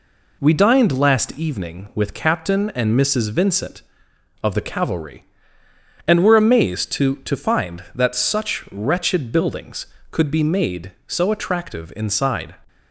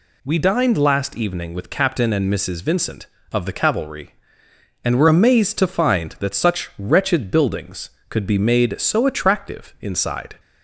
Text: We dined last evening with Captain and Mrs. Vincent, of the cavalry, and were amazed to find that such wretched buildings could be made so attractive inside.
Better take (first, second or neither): second